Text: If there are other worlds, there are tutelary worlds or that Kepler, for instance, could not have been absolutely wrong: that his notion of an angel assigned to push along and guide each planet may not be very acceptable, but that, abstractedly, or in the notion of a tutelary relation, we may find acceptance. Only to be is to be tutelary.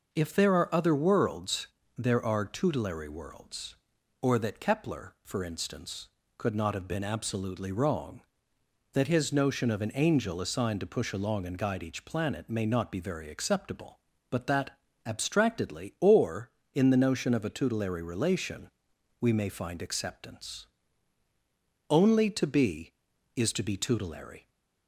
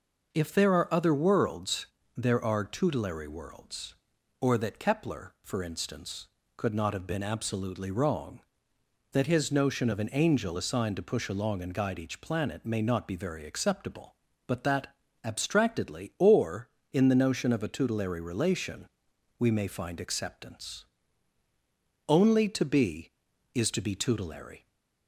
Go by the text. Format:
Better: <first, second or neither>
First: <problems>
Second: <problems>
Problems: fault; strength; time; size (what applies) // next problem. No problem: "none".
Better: neither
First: none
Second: none